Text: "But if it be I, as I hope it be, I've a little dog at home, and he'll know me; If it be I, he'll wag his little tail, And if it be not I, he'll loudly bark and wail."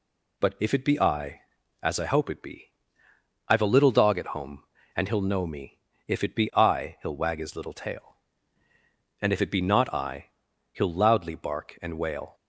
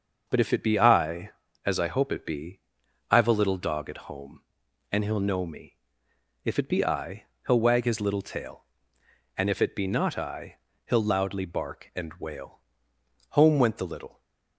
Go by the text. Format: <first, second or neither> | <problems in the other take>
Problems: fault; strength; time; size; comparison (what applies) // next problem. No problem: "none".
first | starts louder than the rest; noticeable; until 1.2 s; 6 dB // goes on to say "Home went the little"; noticeable; from 13.3 s on; 0.88 s long